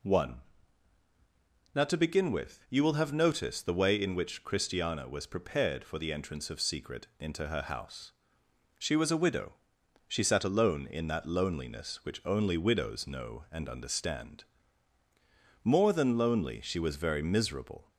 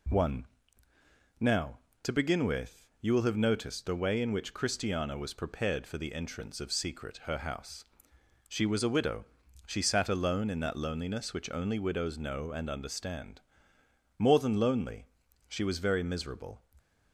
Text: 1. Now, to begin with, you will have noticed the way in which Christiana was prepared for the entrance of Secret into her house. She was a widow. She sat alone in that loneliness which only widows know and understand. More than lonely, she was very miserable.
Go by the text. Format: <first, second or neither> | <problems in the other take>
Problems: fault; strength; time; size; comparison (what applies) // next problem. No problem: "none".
first | skips "into"; at 7.2 s